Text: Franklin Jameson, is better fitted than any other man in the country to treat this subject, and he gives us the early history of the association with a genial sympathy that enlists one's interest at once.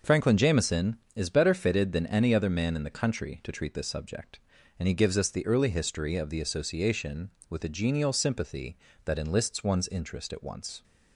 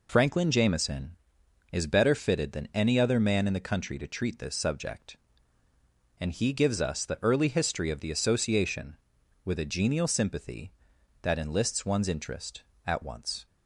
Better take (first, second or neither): neither